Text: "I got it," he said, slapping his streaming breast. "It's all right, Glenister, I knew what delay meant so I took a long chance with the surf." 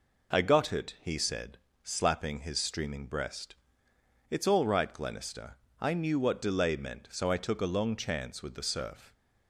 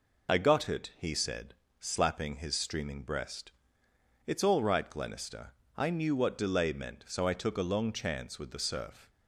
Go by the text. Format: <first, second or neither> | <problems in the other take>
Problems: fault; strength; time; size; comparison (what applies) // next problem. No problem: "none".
first | loses the start of "I"; at 0.2 s; 20 ms